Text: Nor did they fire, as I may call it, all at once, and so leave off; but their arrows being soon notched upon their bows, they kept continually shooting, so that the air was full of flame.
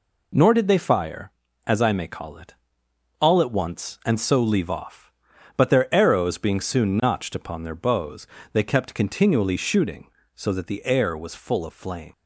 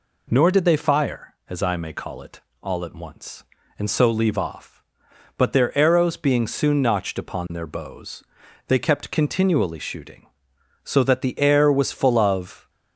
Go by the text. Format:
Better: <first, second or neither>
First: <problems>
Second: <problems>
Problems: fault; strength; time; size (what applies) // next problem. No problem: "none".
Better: first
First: none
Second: stops before "flame"; at 12.6 s